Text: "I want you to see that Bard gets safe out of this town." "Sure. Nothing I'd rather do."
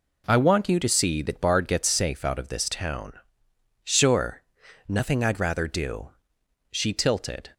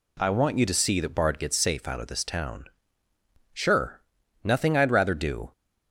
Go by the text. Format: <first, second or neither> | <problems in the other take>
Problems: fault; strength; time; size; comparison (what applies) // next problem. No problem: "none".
second | goes on to say "She tilted"; noticeable; from 6.7 s on; 0.80 s long